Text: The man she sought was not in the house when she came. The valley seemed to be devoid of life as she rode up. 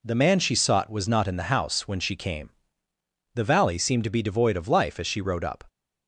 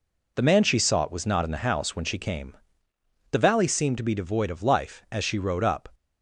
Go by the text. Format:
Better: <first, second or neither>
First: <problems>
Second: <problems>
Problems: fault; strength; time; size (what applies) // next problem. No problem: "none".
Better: neither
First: none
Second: none